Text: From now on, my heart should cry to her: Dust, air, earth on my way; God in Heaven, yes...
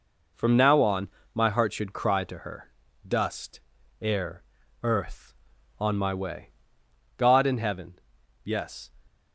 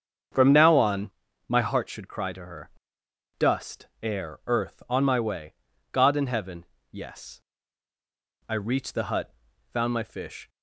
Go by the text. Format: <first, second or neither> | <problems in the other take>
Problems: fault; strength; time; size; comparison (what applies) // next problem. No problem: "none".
first | starts louder than the rest; strong; until 1.6 s; 7.5 dB // goes on to say "I reached the hut found my fish"; strong; from 8.4 s on; 2.0 s long